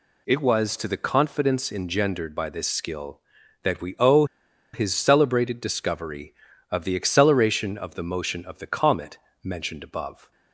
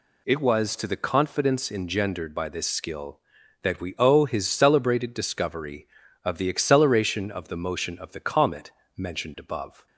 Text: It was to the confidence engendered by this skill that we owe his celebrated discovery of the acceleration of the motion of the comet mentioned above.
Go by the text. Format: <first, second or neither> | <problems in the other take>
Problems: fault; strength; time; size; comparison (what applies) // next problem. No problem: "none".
second | pauses between "owe" and "his"; noticeable; at 4.2 s; 0.49 s long // pauses between "comet" and "mentioned"; slight; at 9.1 s; 0.24 s long; slight in the second